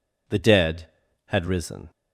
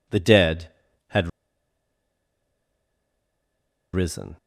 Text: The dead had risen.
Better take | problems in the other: first | pauses between "had" and "risen"; strong; at 1.2 s; 2.6 s long

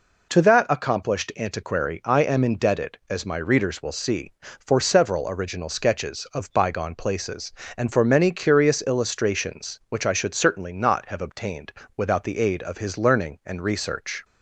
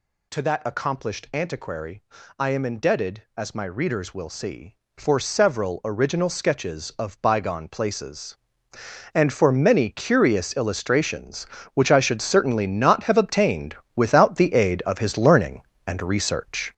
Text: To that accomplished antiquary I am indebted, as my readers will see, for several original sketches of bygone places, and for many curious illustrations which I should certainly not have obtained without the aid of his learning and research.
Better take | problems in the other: first | gets louder; strong; throughout; 7 dB // pauses between "antiquary" and "I"; slight; at 2.0 s; 0.34 s long // pauses between "obtained" and "without"; slight; at 13.7 s; 0.18 s long; slight in the first

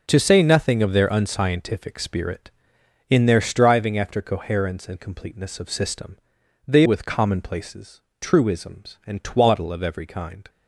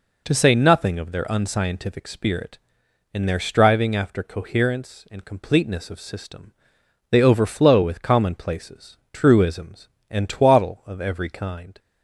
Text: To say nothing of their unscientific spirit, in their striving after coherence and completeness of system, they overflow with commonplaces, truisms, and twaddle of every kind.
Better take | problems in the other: second | skips "overflow"; at 6.8 s

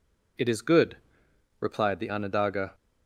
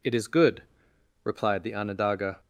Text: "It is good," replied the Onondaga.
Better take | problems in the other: neither | none

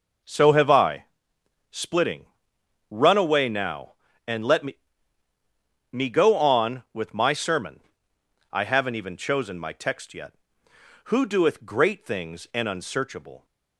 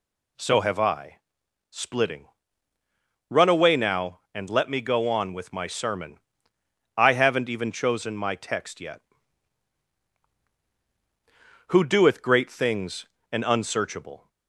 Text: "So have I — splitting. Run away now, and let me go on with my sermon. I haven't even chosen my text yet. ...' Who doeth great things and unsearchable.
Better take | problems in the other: second | says "me" twice; at 5.9 s

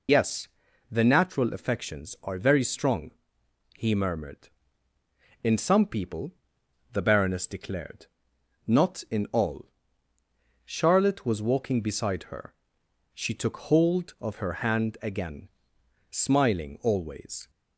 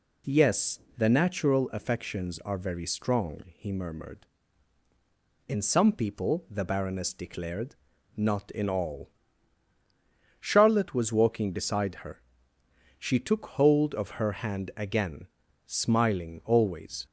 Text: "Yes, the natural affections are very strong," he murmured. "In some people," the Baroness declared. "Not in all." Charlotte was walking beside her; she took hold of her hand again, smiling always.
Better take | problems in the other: second | loses the start of "Yes"; at 0.0 s; 70 ms

